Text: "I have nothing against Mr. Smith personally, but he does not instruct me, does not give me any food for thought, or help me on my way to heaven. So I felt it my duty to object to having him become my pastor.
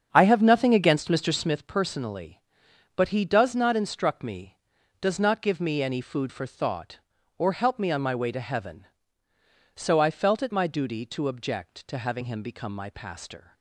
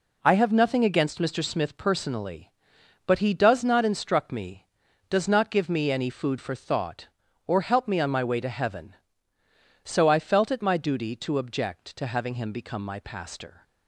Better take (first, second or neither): second